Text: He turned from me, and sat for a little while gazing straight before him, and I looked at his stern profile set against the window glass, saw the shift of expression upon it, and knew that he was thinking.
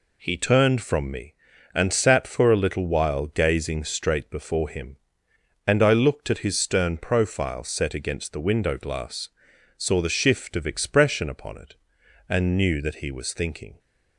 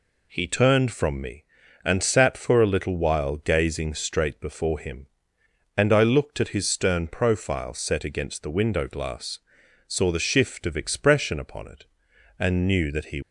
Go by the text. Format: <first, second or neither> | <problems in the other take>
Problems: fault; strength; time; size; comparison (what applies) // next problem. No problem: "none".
first | stops before "was thinking"; at 13.2 s